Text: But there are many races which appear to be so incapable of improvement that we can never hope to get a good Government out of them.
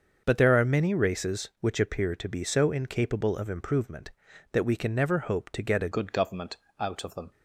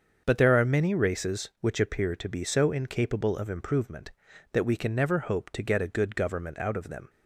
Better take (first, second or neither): second